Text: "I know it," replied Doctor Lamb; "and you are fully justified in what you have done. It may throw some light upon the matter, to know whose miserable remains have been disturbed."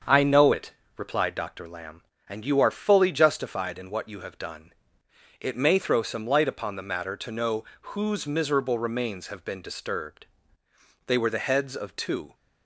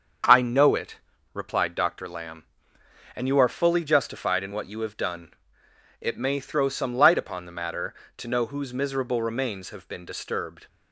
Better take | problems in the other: second | starts louder than the rest; until 1.3 s; 7 dB; also in the second // pauses between "know" and "whose"; slight; at 7.6 s; 0.18 s long // goes on to say "They were the heads of two"; noticeable; from 11.0 s on; 1.2 s long

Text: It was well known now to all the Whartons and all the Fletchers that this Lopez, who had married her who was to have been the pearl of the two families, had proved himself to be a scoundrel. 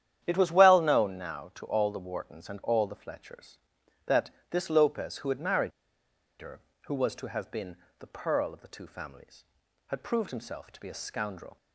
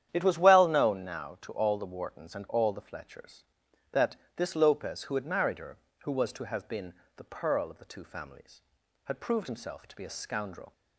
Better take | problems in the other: second | starts louder than the rest; strong; until 1.2 s; 10 dB; strong in the second // pauses between "that" and "this"; slight; at 4.3 s; 0.20 s long; slight in the second // pauses between "married" and "her"; noticeable; at 5.7 s; 0.69 s long // pauses between "been" and "the"; slight; at 7.7 s; 0.22 s long; slight in the second

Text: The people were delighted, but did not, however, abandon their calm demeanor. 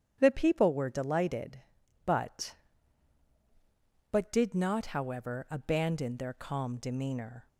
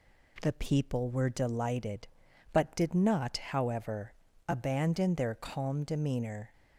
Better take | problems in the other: second | starts louder than the rest; strong; until 1.2 s; 9.5 dB // says "but" twice; at 4.1 s

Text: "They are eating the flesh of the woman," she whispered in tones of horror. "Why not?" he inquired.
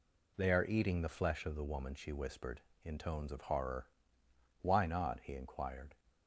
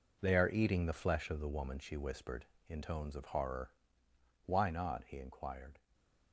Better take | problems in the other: first | gets quieter; strong; throughout; 10 dB // stays silent after the last word; slight; from 5.7 s on; 0.6 s long

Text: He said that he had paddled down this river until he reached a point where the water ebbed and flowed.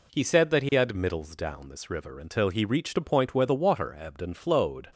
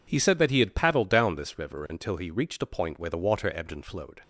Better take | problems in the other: second | says "middles" for "paddled"; at 0.9 s

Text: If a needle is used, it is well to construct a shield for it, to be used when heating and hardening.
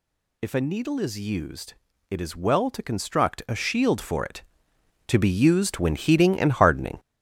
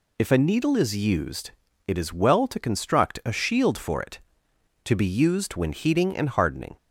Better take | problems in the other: second | gets louder; strong; throughout; 7.5 dB

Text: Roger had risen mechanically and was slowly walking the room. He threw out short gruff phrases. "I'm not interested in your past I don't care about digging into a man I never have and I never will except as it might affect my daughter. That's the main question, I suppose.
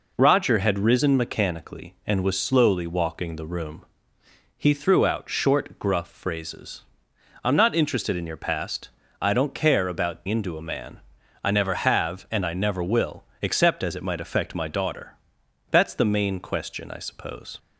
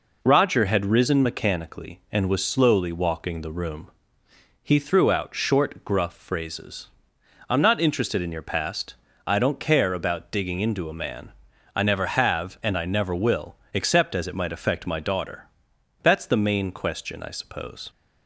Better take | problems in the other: second | pauses between "past" and "I"; slight; at 8.9 s; 0.30 s long; slight in the second // skips "digging"; at 10.2 s // pauses between "man" and "I"; at 10.9 s; 0.44 s long; also in the second // pauses between "will" and "except"; slight; at 13.2 s; 0.16 s long; slight in the second

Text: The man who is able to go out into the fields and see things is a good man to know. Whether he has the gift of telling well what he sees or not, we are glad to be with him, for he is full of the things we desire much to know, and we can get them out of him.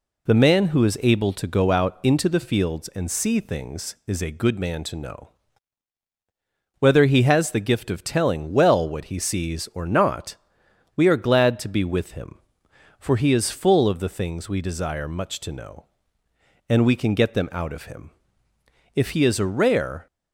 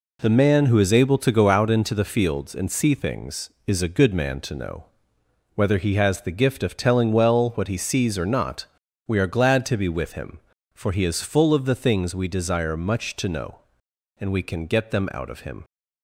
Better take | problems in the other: second | goes on to say "If he is a rare"; noticeable; from 18.9 s on; 1.1 s long

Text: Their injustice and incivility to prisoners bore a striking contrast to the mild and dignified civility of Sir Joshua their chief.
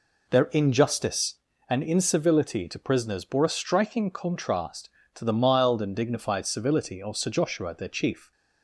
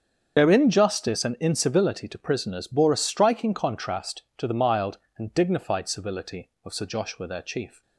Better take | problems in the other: first | loses the start of "Their"; at 0.3 s; 55 ms // starts louder than the rest; strong; until 1.4 s; 7.5 dB

